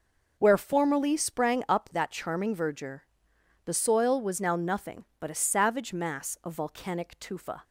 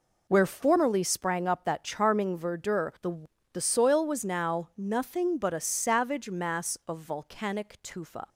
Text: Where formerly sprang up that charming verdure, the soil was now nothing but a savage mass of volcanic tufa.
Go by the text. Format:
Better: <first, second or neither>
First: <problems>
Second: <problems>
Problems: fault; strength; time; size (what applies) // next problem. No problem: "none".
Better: first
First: none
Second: says "the" twice; at 3.5 s